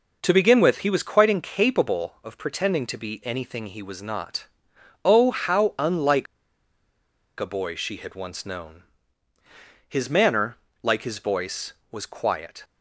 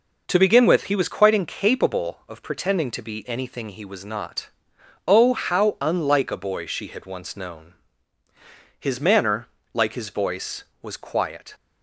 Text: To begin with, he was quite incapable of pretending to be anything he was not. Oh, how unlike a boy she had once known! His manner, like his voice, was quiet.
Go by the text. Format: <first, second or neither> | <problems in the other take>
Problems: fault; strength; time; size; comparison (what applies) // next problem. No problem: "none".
second | pauses between "unlike" and "a"; at 6.2 s; 1.1 s long